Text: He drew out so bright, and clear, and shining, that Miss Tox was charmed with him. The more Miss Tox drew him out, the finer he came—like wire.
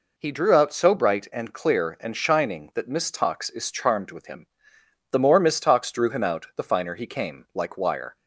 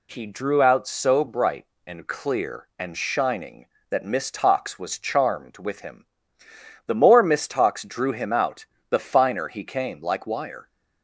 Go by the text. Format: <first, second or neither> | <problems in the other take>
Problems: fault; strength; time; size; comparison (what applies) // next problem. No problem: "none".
second | says "is" for "was"; at 3.4 s